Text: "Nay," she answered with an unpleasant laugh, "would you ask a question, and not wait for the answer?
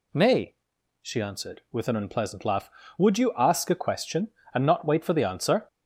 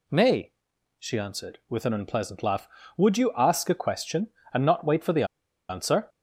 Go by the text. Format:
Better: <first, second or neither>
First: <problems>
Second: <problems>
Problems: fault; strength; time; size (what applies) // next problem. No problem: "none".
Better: first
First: none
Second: pauses between "the" and "answer"; at 5.2 s; 0.44 s long